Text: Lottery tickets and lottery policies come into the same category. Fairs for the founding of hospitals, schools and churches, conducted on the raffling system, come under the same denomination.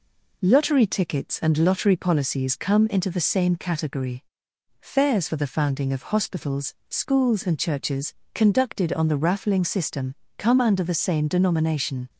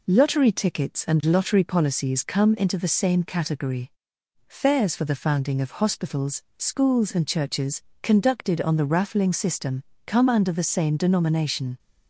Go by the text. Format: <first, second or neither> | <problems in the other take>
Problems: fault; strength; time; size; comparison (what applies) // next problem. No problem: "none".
neither | none